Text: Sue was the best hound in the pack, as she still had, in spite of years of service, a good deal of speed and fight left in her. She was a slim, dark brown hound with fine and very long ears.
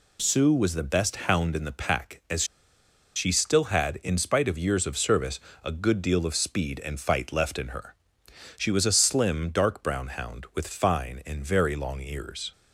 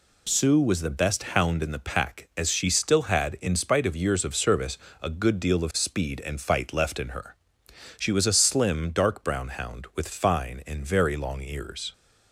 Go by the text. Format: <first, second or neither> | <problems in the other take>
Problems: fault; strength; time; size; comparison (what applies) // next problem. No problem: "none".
second | pauses between "as" and "she"; noticeable; at 2.4 s; 0.71 s long